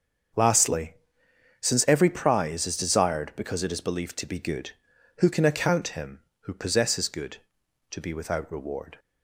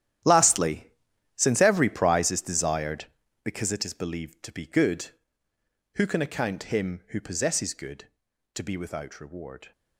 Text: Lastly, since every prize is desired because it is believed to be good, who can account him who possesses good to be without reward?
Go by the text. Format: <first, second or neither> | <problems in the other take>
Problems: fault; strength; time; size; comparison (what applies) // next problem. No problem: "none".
first | gets quieter; strong; throughout; 14.5 dB // starts louder than the rest; strong; until 1.7 s; 11.5 dB; also in the first